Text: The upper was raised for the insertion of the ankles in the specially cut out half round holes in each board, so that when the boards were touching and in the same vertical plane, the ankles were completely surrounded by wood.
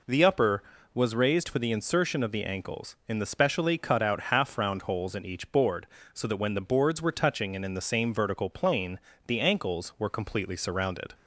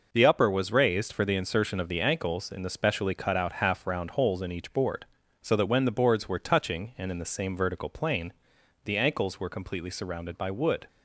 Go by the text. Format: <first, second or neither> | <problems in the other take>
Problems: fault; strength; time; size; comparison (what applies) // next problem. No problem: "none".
second | stops before "by wood"; at 11.1 s